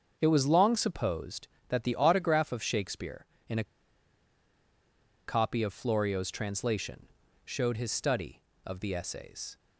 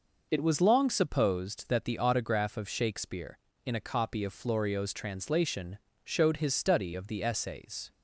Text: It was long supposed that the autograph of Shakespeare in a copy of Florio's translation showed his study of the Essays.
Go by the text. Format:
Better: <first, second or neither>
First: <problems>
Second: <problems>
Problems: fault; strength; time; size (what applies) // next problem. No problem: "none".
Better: second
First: starts louder than the rest; until 1.2 s; 6.5 dB // pauses between "a" and "copy"; strong; at 3.6 s; 1.6 s long // pauses between "translation" and "showed"; at 7.0 s; 0.38 s long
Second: pauses between "translation" and "showed"; slight; at 5.7 s; 0.26 s long